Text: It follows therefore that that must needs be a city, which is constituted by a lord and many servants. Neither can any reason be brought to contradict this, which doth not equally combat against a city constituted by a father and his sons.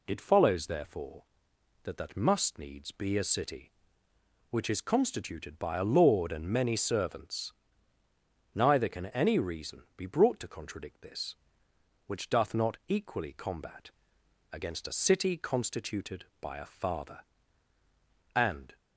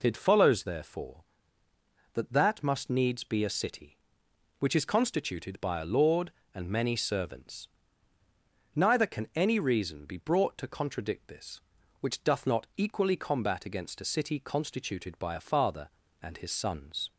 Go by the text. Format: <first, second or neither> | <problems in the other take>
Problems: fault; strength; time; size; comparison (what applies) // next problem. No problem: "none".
second | pauses between "combat" and "against"; noticeable; at 13.8 s; 0.62 s long // stops before "his sons"; at 18.7 s